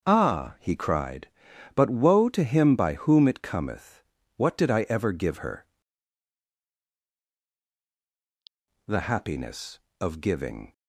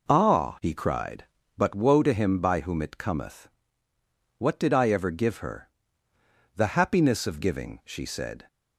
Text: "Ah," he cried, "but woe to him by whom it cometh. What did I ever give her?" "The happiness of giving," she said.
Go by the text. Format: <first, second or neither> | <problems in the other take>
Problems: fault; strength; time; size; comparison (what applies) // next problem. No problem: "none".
second | starts louder than the rest; noticeable; until 1.0 s; 6 dB // stops before "she said"; at 10.7 s